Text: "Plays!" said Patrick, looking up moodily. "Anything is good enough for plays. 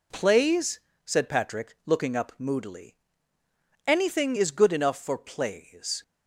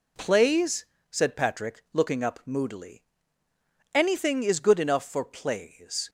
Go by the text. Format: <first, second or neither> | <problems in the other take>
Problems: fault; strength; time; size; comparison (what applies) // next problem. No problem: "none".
neither | none